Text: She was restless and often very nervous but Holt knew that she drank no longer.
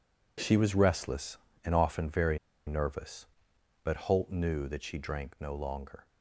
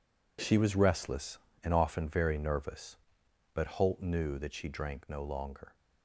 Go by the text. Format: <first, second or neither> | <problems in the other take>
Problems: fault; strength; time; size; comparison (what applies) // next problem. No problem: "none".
second | pauses between "very" and "nervous"; slight; at 2.3 s; 0.29 s long